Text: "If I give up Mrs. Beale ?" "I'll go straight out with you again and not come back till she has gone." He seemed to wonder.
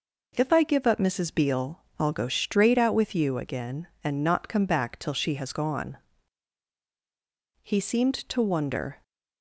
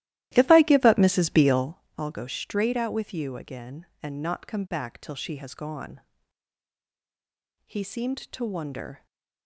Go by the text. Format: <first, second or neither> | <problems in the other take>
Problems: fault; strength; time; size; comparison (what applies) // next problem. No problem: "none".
first | starts louder than the rest; strong; until 1.9 s; 14.5 dB